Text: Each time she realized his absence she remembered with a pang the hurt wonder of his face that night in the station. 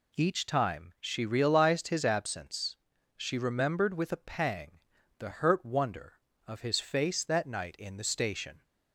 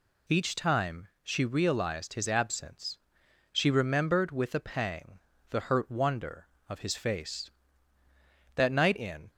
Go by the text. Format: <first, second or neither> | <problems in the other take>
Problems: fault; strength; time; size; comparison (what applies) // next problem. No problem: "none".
first | pauses between "time" and "she"; slight; at 1.0 s; 0.16 s long // pauses between "absence" and "she"; noticeable; at 2.9 s; 0.56 s long; also in the first // pauses between "pang" and "the"; slight; at 5.1 s; 0.32 s long; also in the first // stops before "the station"; at 9.3 s